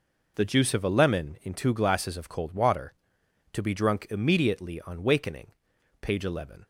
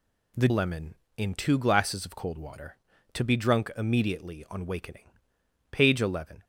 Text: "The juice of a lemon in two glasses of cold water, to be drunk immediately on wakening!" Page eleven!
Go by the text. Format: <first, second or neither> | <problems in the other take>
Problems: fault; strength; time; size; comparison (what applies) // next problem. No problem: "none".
first | skips "juice of a"; at 0.4 s